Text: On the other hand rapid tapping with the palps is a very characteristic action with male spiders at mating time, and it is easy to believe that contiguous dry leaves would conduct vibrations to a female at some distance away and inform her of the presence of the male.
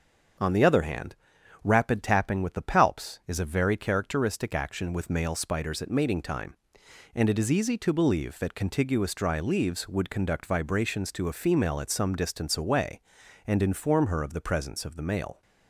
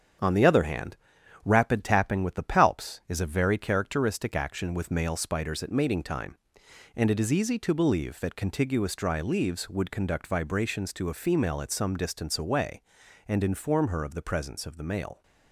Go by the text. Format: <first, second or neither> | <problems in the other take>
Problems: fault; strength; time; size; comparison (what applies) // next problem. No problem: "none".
first | gets quieter; noticeable; throughout; 5 dB // starts louder than the rest; strong; until 1.6 s; 8 dB; also in the first // pauses between "hand" and "rapid"; noticeable; at 0.9 s; 0.48 s long; noticeable in the first